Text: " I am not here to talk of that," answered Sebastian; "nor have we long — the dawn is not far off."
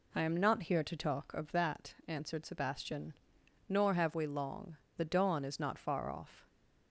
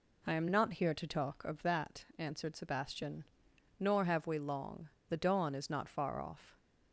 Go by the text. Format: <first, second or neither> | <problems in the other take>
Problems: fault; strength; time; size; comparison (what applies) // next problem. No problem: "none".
neither | none